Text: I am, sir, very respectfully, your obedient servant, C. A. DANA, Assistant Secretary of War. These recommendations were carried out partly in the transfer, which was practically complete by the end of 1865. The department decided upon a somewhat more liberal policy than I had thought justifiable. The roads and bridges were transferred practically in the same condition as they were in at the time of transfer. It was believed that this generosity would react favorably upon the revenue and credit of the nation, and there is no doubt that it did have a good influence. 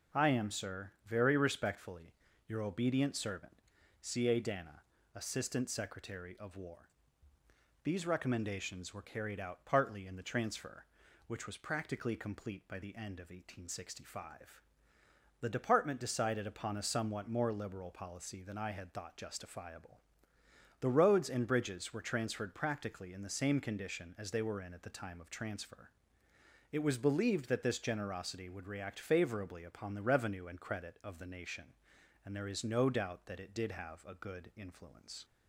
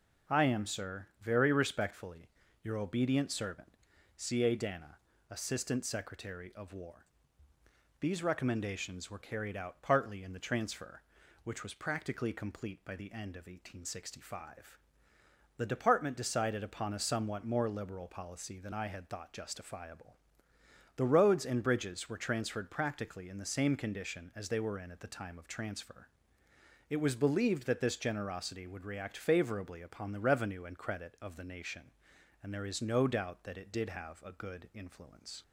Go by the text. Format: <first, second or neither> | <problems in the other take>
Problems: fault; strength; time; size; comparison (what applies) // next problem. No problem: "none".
neither | none